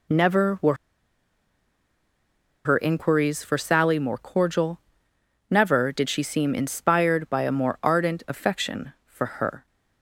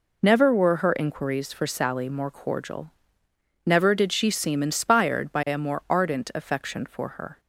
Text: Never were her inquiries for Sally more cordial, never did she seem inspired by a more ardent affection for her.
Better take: second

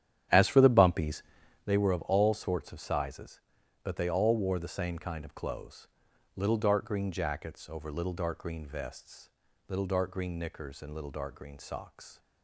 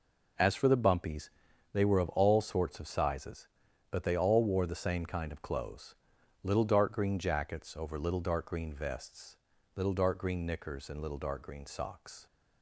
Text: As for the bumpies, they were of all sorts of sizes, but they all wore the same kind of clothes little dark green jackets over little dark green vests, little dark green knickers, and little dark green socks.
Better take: second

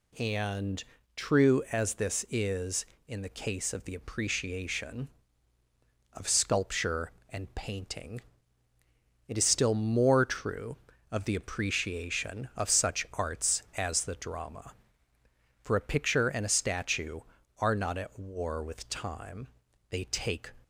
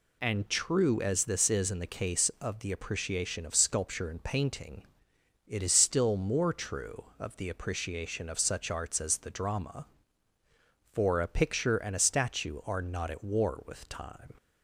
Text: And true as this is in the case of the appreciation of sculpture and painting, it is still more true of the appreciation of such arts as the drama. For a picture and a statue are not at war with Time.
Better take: second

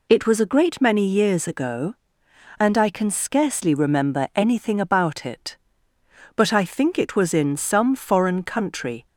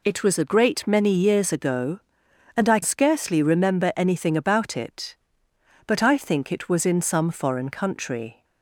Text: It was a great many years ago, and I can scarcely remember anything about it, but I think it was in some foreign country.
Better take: first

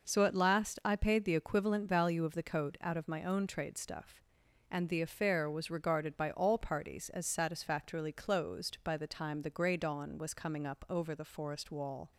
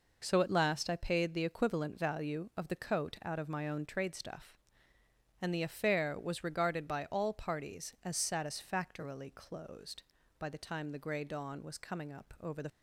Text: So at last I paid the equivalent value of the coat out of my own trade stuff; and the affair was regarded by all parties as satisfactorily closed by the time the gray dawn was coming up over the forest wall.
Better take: first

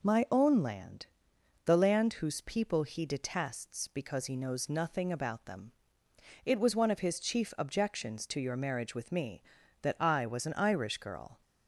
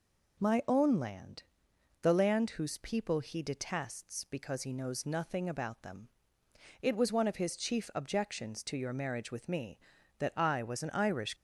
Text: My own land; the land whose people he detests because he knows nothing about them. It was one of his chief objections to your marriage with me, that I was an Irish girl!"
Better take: first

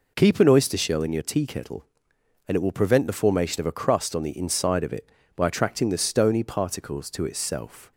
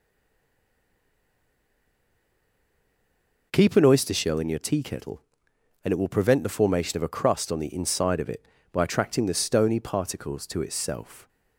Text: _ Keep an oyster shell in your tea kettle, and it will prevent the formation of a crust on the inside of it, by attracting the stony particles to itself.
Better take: first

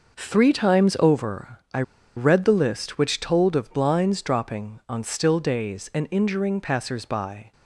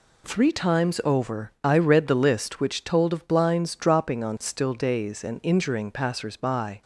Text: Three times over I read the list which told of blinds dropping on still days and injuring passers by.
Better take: second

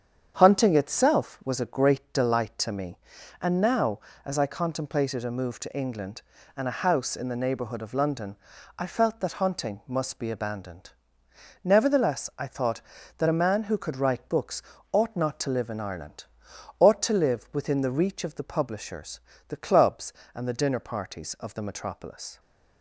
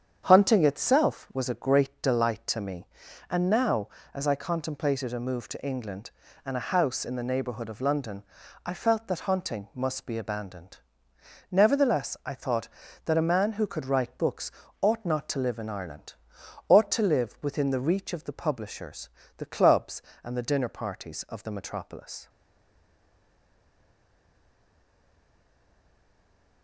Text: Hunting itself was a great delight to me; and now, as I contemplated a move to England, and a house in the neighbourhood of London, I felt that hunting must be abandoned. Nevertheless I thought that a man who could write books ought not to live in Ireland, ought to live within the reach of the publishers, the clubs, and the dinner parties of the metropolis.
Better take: first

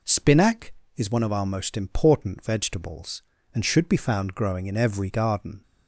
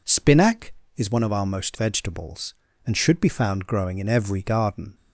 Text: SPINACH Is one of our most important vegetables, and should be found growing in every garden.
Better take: first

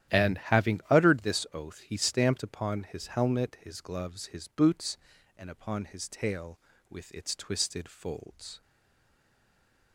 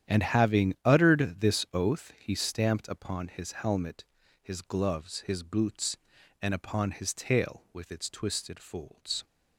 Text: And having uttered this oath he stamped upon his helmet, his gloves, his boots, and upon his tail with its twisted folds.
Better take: second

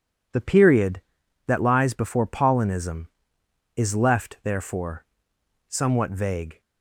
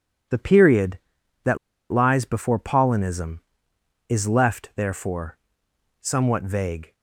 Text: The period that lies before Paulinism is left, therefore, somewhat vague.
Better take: first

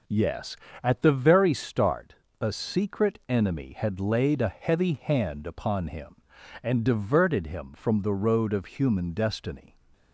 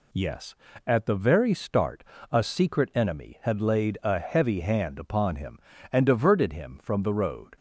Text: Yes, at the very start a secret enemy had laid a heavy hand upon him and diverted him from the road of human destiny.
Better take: first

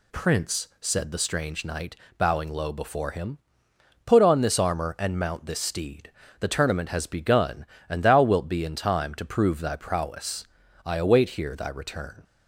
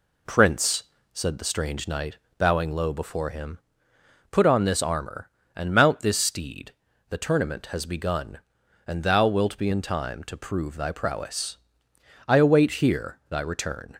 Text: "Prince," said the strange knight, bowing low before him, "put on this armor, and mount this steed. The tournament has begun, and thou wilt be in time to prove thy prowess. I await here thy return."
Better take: neither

